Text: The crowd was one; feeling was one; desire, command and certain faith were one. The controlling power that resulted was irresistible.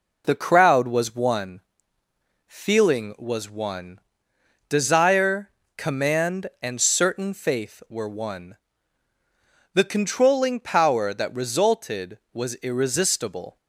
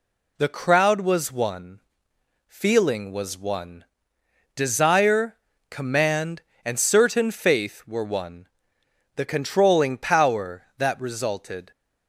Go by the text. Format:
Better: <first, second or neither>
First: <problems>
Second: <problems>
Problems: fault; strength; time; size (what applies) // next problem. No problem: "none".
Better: first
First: none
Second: stops before "was irresistible"; at 11.7 s